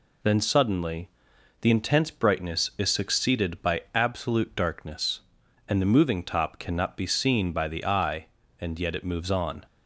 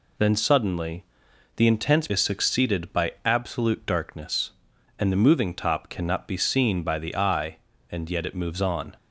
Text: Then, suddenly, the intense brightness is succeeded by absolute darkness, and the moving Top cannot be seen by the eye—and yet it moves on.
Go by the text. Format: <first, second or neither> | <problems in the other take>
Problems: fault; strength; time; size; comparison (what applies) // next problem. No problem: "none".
first | skips "brightness"; at 2.0 s